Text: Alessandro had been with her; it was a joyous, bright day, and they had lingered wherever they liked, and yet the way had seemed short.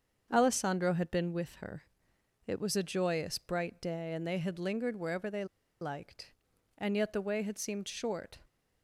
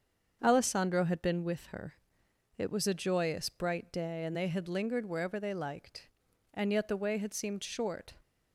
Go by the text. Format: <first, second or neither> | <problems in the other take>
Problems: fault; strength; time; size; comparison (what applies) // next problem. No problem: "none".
second | starts louder than the rest; until 1.3 s; 7 dB; also in the second // pauses between "they" and "liked"; slight; at 5.4 s; 0.36 s long